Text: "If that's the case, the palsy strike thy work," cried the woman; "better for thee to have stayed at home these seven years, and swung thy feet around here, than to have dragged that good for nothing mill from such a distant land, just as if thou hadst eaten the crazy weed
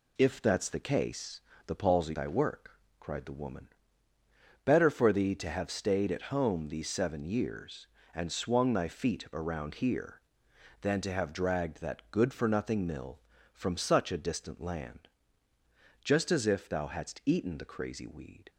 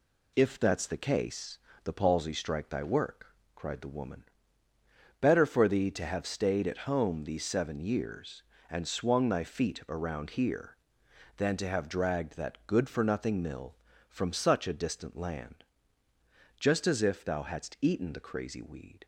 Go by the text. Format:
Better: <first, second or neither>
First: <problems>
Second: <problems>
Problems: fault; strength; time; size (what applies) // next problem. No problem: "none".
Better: second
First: skips "strike"; at 2.1 s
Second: none